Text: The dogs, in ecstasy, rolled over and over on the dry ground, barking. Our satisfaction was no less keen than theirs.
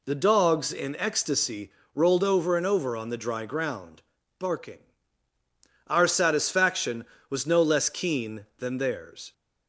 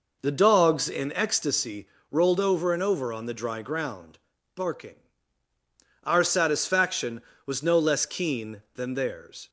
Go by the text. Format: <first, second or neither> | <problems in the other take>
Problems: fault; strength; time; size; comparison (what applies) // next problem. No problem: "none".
first | starts louder than the rest; noticeable; until 1.5 s; 5 dB